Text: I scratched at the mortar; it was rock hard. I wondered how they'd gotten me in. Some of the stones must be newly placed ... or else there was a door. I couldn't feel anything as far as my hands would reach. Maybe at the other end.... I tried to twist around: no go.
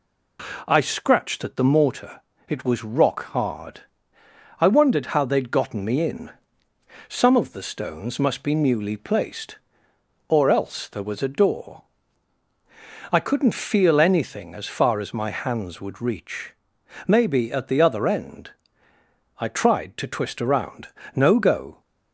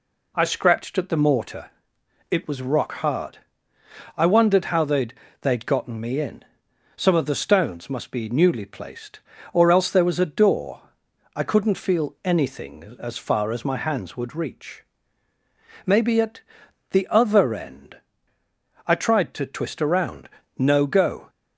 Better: first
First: none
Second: says "they'd" twice; at 5.4 s // pauses between "at" and "the"; noticeable; at 16.4 s; 0.48 s long

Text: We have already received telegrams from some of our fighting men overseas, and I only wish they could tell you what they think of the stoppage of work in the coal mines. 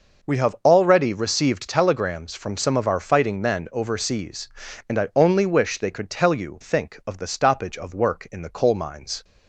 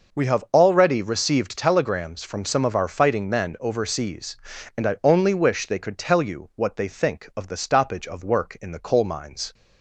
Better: second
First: skips "what they"; at 6.6 s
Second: none

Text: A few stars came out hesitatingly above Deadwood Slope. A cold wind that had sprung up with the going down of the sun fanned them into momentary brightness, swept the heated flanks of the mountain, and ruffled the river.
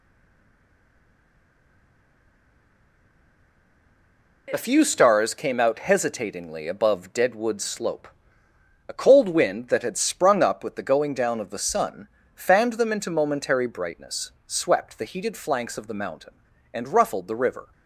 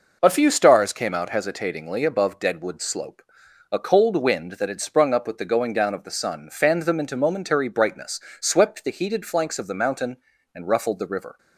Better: second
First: stays silent before the first word; strong; until 4.4 s; 4.4 s long // pauses between "sun" and "fanned"; slight; at 12.0 s; 0.28 s long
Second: none

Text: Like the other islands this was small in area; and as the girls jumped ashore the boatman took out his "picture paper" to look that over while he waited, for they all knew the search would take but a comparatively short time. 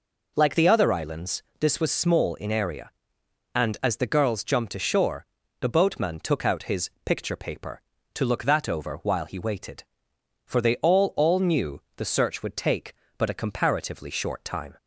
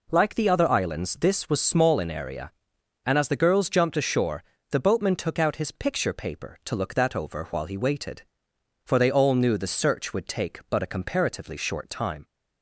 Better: second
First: pauses between "islands" and "this"; slight; at 1.4 s; 0.16 s long // pauses between "ashore" and "the"; slight; at 5.2 s; 0.34 s long // says "all" twice; at 11.1 s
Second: pauses between "ashore" and "the"; slight; at 4.4 s; 0.28 s long

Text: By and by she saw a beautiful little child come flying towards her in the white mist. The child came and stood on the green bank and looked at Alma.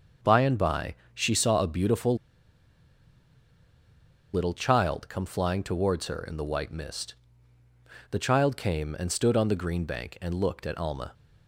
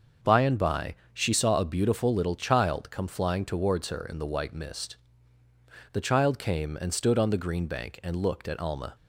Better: second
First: starts louder than the rest; until 1.4 s; 6.5 dB // pauses between "by" and "she"; slight; at 0.9 s; 0.22 s long // pauses between "beautiful" and "little"; strong; at 2.1 s; 2.1 s long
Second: starts louder than the rest; until 1.4 s; 6.5 dB // pauses between "by" and "she"; slight; at 0.9 s; 0.21 s long

